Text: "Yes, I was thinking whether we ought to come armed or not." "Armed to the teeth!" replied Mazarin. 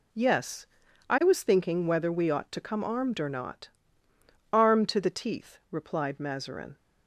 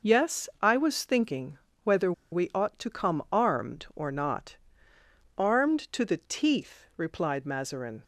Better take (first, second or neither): first